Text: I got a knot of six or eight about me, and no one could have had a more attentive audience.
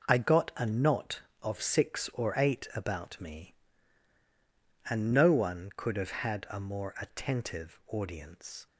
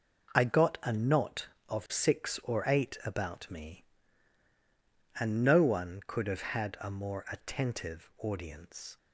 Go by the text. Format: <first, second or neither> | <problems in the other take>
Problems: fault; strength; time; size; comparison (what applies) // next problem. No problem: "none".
neither | none